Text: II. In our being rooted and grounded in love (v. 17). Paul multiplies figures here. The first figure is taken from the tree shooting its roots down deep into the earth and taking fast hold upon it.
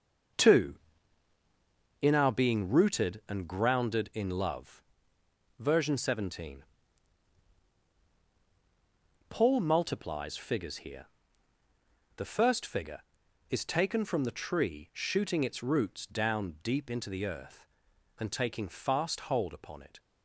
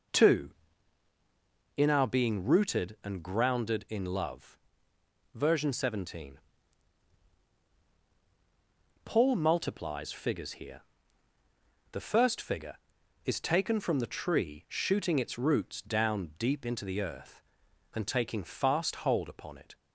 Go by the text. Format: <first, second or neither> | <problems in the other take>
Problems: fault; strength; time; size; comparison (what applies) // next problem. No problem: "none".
second | gets quieter; strong; throughout; 7.5 dB